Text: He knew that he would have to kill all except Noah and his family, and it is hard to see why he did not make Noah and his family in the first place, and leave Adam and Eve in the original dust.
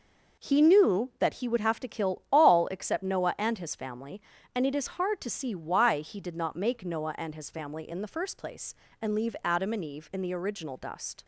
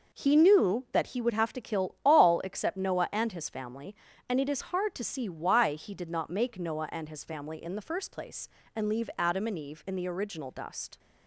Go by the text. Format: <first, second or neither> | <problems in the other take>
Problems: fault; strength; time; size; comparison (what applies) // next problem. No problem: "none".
neither | none